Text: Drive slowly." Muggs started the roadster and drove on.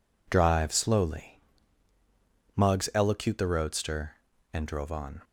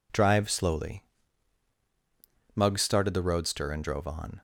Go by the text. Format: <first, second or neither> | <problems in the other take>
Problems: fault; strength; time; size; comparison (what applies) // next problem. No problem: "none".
second | says "elocute" for "started"; at 2.9 s